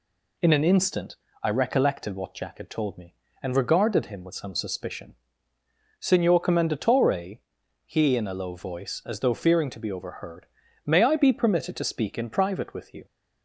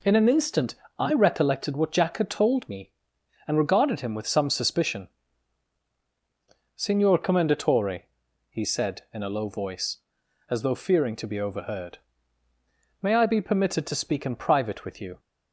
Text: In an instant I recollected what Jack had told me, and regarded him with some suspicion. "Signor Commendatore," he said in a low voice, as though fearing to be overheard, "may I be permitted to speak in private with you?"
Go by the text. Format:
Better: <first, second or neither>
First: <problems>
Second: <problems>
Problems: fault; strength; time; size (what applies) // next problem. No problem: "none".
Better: second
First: pauses between "instant" and "I"; slight; at 1.1 s; 0.28 s long // skips "said"; at 8.1 s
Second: pauses between "instant" and "I"; slight; at 0.7 s; 0.24 s long